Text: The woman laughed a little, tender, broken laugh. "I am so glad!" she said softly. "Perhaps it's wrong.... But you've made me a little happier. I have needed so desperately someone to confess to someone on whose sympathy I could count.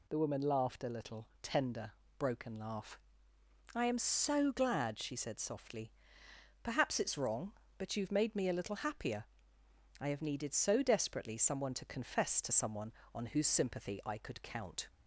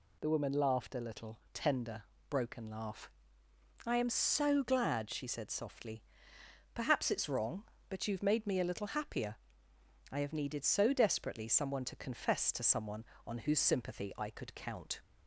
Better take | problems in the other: neither | none

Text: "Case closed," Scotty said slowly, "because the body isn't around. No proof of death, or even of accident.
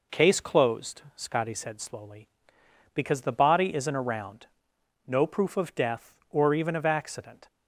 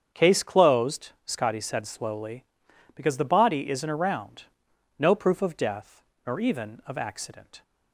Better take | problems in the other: first | starts louder than the rest; strong; until 1.2 s; 8 dB // says "nor" for "or"; at 6.2 s

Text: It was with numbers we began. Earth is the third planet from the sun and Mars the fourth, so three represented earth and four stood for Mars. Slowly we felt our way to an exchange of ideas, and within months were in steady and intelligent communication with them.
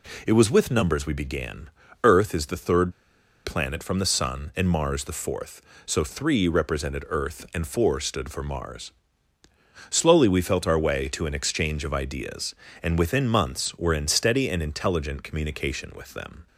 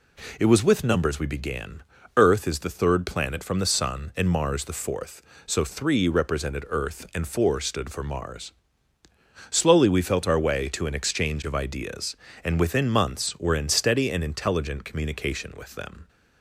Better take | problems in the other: second | pauses between "third" and "planet"; noticeable; at 2.9 s; 0.52 s long

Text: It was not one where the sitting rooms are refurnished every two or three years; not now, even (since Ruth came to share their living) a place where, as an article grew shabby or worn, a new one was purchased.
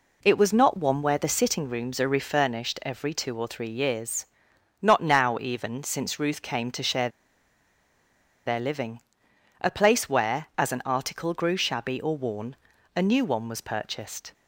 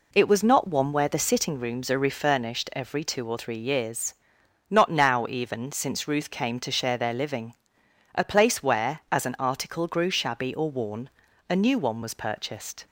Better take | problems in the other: second | pauses between "share" and "their"; strong; at 7.0 s; 1.3 s long

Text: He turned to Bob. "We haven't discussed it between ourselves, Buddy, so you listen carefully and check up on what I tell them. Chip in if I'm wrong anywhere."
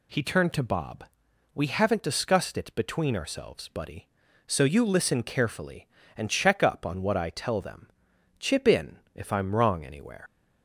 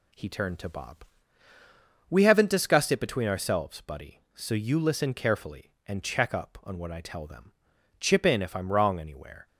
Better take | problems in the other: second | pauses between "in" and "if"; slight; at 8.9 s; 0.16 s long // leaves "anywhere" unfinished; at 10.2 s; 80 ms

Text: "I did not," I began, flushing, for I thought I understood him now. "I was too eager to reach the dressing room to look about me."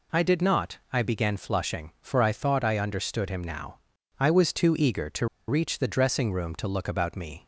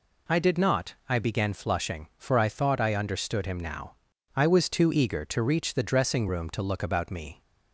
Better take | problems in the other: second | pauses between "to" and "reach"; slight; at 5.2 s; 0.22 s long

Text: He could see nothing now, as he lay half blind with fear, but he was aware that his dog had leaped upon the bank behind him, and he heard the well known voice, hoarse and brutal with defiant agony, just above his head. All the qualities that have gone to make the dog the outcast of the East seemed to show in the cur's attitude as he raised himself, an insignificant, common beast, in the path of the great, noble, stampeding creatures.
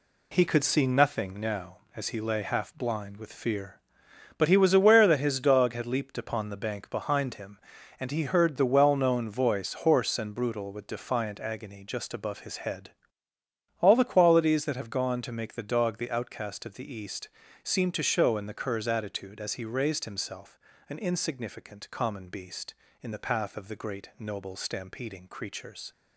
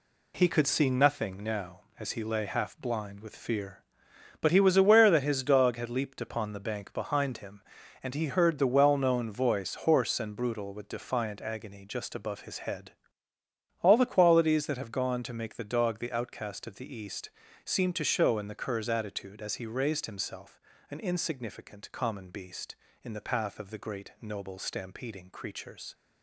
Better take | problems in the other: neither | pauses between "East" and "seemed"; slight; the same in both

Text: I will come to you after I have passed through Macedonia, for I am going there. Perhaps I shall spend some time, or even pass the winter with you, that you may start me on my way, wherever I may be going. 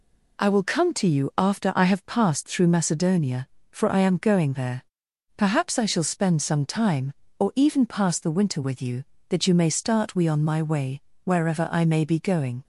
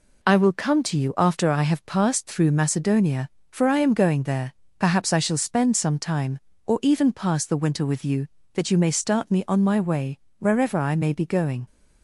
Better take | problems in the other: second | says "we" for "me"; at 10.1 s

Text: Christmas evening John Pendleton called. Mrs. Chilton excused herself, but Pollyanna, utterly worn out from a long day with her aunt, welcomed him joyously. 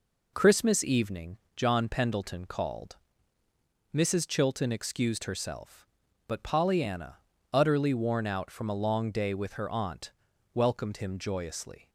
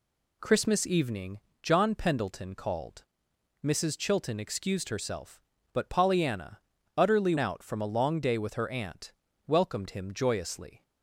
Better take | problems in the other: first | pauses between "evening" and "John"; slight; at 1.3 s; 0.24 s long; slight in the first // skips "worn"; at 7.3 s

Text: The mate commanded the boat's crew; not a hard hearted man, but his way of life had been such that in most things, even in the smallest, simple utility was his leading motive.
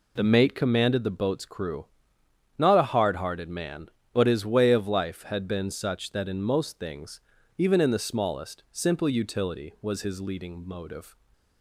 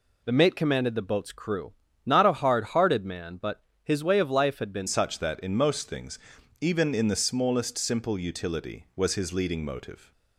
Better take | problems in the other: first | pauses between "but" and "his"; slight; at 3.6 s; 0.20 s long // changes voice at "such"; from 4.8 s on; 5.3 s long

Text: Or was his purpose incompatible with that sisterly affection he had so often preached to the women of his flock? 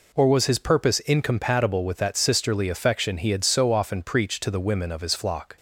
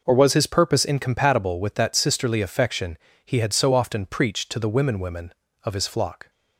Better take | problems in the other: first | pauses between "affection" and "he"; slight; at 2.9 s; 0.26 s long // says "women" twice; at 4.9 s

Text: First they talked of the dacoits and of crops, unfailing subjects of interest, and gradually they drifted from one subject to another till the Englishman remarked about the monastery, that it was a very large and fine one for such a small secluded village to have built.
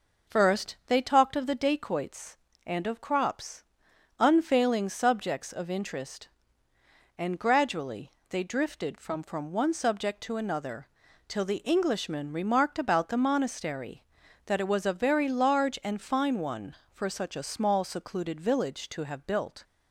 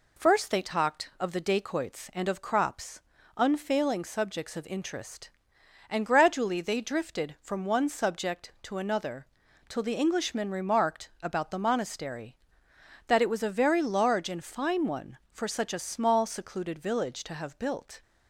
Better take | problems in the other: second | pauses between "gradually" and "they"; slight; at 8.1 s; 0.18 s long // says "from" twice; at 9.2 s // pauses between "another" and "till"; at 10.8 s; 0.40 s long; also in the second

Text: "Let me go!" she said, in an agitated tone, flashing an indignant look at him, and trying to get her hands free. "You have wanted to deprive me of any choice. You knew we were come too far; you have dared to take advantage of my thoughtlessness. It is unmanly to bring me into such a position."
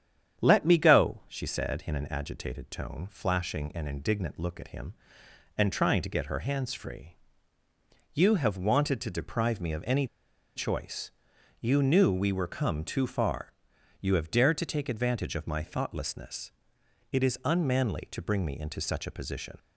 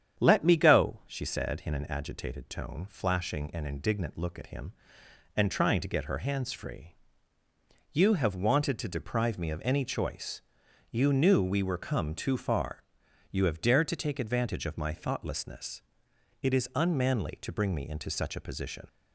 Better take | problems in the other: second | starts louder than the rest; strong; until 1.4 s; 8.5 dB; strong in the second // pauses between "any" and "choice"; noticeable; at 10.0 s; 0.50 s long

